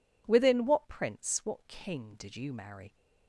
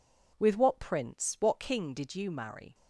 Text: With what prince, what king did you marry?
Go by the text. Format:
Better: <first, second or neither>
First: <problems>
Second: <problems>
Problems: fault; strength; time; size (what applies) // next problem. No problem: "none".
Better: second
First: says "Within" for "With"; at 0.2 s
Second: none